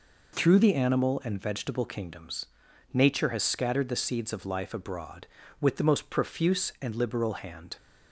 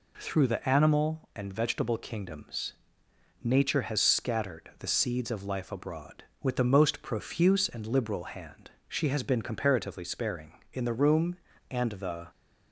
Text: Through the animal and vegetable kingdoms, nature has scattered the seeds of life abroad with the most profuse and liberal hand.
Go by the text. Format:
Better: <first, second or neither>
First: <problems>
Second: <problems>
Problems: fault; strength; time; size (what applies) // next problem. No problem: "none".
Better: first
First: none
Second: goes on to say "She has been comparatively sparing in the room and the"; strong; from 8.8 s on; 3.4 s long